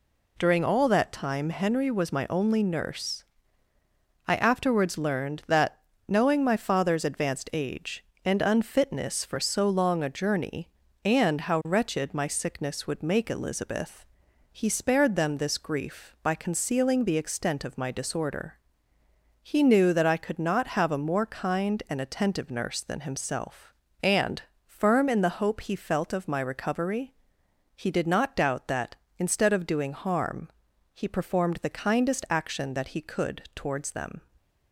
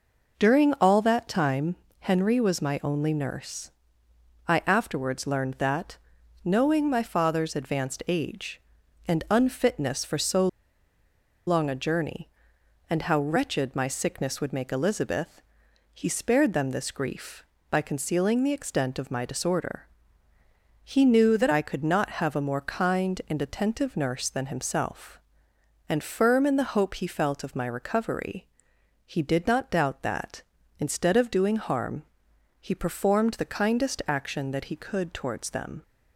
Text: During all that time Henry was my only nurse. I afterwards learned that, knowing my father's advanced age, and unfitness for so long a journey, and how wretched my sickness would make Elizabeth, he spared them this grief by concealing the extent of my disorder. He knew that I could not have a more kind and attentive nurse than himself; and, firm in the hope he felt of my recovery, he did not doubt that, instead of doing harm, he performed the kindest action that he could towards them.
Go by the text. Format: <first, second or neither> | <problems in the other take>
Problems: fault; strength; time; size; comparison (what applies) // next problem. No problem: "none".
first | pauses between "time" and "Henry"; slight; at 1.7 s; 0.26 s long // pauses between "so" and "long"; at 10.4 s; 1.0 s long